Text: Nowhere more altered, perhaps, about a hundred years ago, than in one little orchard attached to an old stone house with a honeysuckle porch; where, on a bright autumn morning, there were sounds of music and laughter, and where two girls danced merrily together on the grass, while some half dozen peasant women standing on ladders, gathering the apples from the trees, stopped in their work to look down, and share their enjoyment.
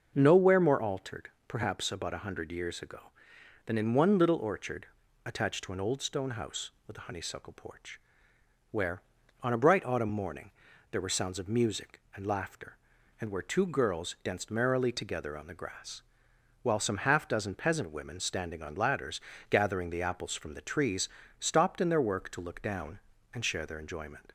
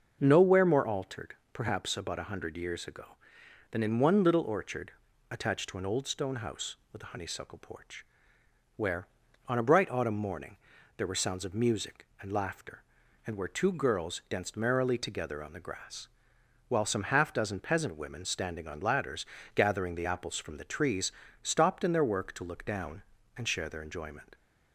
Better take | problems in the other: neither | starts louder than the rest; noticeable; the same in both // pauses between "orchard" and "attached"; the same in both

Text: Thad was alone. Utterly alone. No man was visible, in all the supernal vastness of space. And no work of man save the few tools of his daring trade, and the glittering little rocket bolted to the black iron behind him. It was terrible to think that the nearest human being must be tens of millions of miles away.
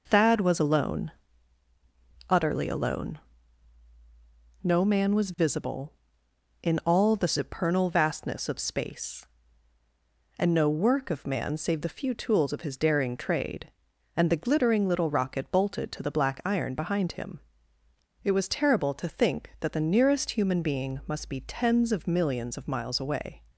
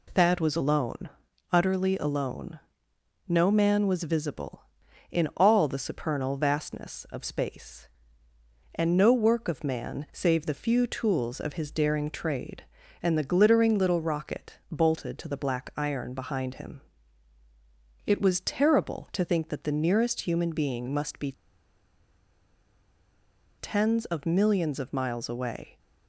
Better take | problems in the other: first | pauses between "be" and "tens"; strong; at 21.3 s; 2.2 s long

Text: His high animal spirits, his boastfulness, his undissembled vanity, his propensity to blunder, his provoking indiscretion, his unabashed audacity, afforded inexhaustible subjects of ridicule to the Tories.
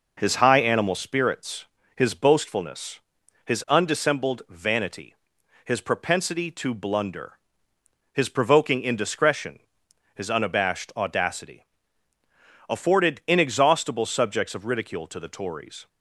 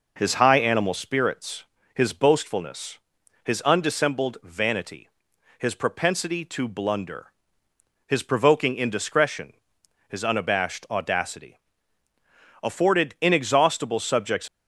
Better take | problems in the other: first | stops before "of ridicule to the Tories"; at 14.4 s

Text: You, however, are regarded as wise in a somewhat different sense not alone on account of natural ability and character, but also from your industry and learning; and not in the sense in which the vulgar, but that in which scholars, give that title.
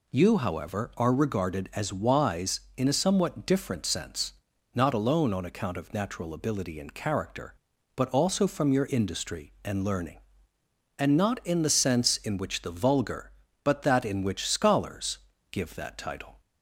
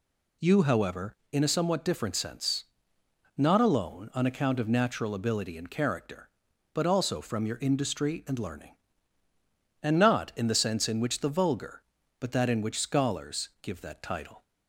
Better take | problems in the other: first | skips "are regarded as wise"; at 1.2 s // pauses between "sense" and "not"; noticeable; at 2.6 s; 0.74 s long; also in the first

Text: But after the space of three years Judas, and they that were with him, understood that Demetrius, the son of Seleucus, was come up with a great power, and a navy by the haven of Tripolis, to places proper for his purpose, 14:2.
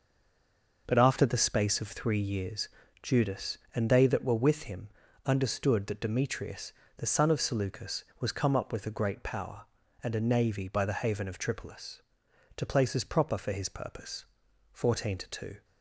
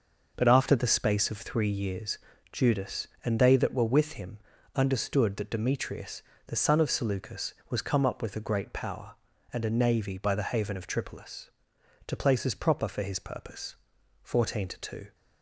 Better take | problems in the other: second | stays silent before the first word; slight; until 0.8 s; 0.8 s long // pauses between "years" and "Judas"; slight; at 2.6 s; 0.34 s long; slight in the second

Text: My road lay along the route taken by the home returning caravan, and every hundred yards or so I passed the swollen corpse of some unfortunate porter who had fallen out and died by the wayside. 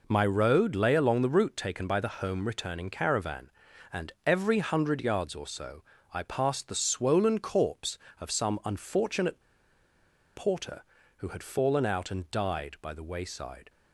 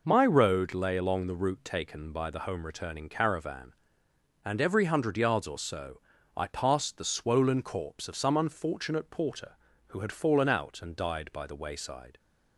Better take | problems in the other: second | pauses between "so" and "I"; slight; at 5.8 s; 0.30 s long; also in the second // pauses between "unfortunate" and "porter"; noticeable; at 9.4 s; 0.94 s long

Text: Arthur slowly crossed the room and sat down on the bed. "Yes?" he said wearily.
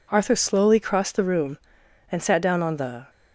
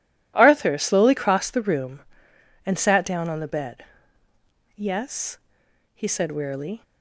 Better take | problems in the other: second | stops before "bed Yes he said wearily"; at 3.0 s

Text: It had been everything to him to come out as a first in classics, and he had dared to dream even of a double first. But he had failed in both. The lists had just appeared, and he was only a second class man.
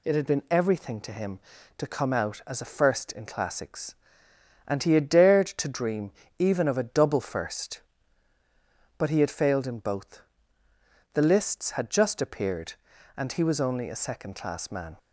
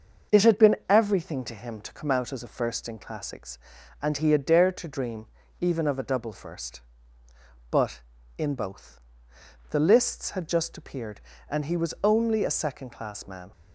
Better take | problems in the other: first | starts louder than the rest; until 1.4 s; 6 dB // pauses between "dream" and "even"; slight; at 5.2 s; 0.34 s long; slight in the first // skips "he had failed"; at 8.1 s

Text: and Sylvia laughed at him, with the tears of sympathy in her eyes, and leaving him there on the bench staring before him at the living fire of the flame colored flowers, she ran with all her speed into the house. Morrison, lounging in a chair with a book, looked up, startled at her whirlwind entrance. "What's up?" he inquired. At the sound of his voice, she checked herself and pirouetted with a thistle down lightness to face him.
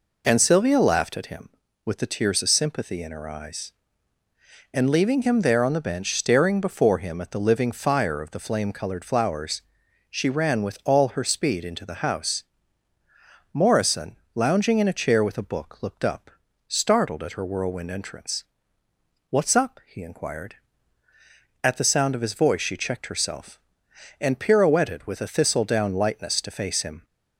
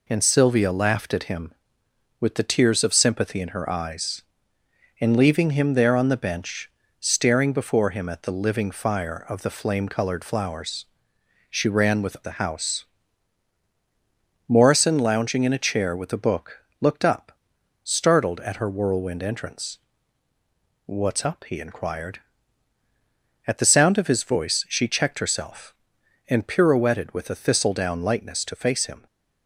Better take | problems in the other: first | pauses between "bench" and "staring"; slight; at 6.7 s; 0.28 s long // skips "all her speed into"; at 12.2 s

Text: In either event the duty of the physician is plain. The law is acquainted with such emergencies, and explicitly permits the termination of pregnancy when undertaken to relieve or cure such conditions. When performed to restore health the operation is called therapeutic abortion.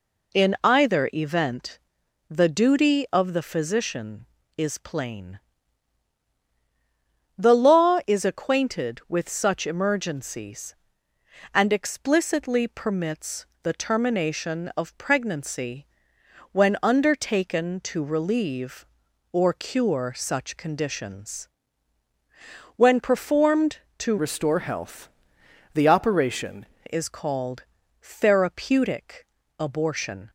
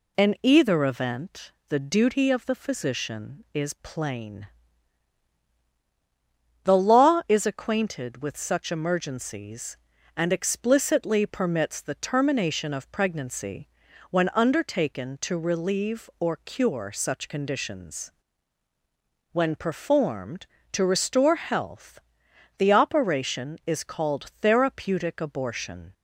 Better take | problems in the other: second | pauses between "event" and "the"; noticeable; at 1.7 s; 0.50 s long; slight in the second // pauses between "permits" and "the"; slight; at 13.4 s; 0.18 s long // pauses between "pregnancy" and "when"; noticeable; at 15.8 s; 0.64 s long; also in the second // changes voice from "restore" to "operation"; from 24.1 to 26.6 s; 2.5 s long // pauses between "health" and "the"; noticeable; at 25.0 s; 0.66 s long; noticeable in the second // pauses between "called" and "therapeutic"; at 27.6 s; 0.38 s long // pauses between "therapeutic" and "abortion"; slight; at 29.2 s; 0.36 s long

